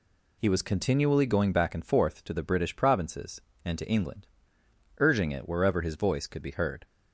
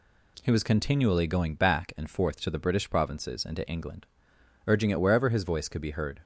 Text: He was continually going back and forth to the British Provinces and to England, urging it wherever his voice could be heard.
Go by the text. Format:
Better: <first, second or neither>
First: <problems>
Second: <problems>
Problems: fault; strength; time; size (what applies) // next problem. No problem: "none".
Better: neither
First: none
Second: none